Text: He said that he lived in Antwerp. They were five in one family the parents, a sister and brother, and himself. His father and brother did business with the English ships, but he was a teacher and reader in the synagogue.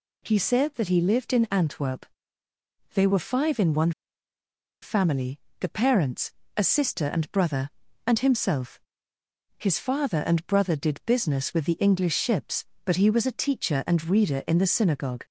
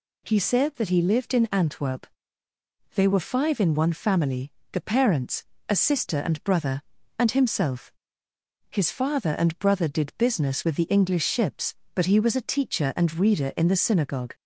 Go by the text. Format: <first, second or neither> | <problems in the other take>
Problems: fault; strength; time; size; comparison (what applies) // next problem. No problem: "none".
second | pauses between "one" and "family"; noticeable; at 3.9 s; 0.91 s long // pauses between "family" and "the"; slight; at 5.3 s; 0.20 s long; slight in the second